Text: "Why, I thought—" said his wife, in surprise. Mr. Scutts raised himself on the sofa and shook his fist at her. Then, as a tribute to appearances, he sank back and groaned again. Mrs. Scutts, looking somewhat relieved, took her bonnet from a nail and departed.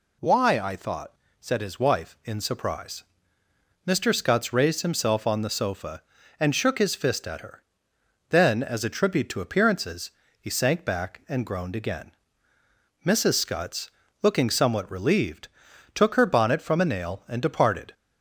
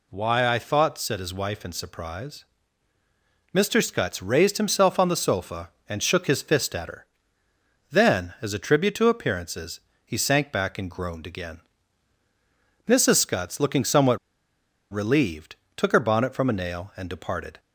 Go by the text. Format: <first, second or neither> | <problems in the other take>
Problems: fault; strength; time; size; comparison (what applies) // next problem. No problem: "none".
first | pauses between "somewhat" and "relieved"; noticeable; at 14.1 s; 0.74 s long